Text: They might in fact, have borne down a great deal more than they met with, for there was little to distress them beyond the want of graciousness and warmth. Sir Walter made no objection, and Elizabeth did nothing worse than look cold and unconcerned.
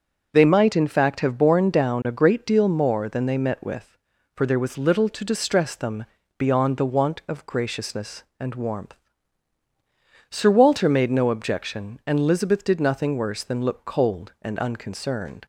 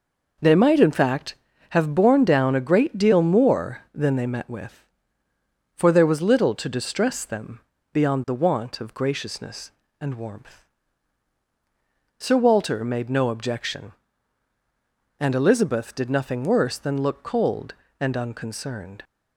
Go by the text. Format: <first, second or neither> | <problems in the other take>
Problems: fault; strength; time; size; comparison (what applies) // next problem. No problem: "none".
neither | pauses between "them" and "beyond"; slight; the same in both